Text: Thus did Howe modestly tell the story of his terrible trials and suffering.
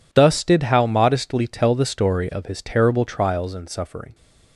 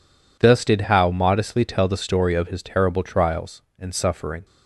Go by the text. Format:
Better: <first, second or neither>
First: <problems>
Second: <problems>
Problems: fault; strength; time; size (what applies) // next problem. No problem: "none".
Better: neither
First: none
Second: none